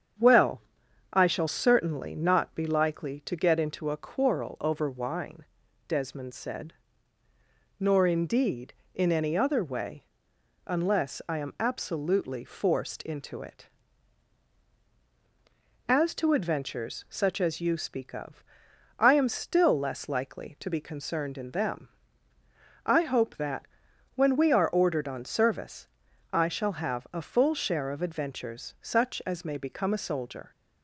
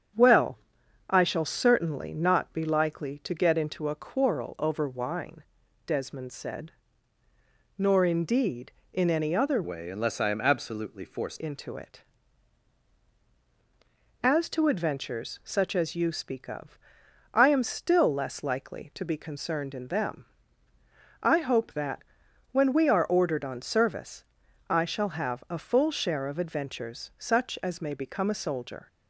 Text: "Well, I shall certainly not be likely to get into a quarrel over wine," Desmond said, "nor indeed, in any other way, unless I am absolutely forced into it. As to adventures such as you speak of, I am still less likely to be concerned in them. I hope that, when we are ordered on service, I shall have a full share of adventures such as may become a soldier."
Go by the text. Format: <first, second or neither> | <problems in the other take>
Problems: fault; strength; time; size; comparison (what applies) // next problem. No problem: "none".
first | starts louder than the rest; strong; until 1.6 s; 7.5 dB; strong in the first // changes voice from "way" to "forced"; from 9.6 to 11.4 s; 1.8 s long